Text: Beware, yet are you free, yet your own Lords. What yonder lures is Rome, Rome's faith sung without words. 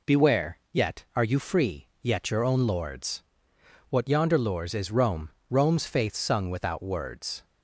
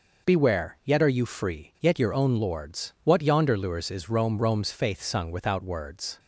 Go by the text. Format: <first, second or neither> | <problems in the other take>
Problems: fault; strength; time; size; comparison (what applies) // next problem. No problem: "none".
neither | none